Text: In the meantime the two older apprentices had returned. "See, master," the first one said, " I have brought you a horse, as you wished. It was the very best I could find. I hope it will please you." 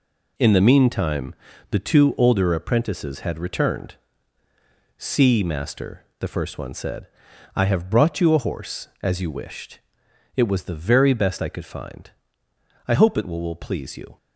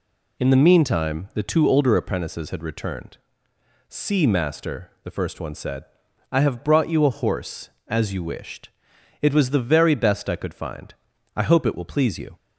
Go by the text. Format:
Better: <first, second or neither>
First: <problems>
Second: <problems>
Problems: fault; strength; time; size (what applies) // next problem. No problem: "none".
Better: second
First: pauses between "meantime" and "the"; slight; at 1.3 s; 0.36 s long // says "will" twice; at 13.4 s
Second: none